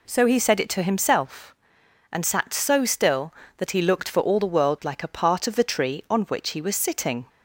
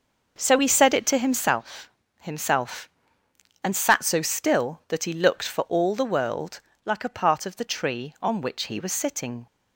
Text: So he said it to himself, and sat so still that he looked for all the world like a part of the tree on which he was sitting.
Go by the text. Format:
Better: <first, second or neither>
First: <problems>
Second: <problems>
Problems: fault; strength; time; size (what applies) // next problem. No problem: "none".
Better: first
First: none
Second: says "himself" twice; at 2.1 s // pauses between "world" and "like"; slight; at 6.5 s; 0.24 s long